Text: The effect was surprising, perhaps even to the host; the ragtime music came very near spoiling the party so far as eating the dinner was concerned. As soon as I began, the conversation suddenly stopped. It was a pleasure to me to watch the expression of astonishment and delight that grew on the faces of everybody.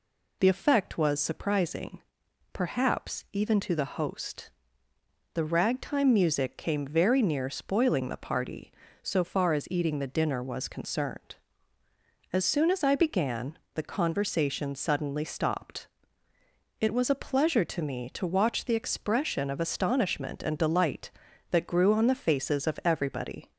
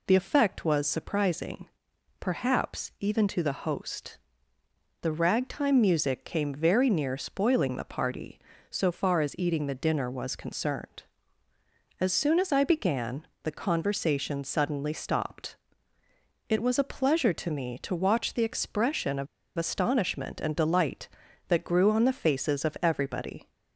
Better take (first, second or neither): first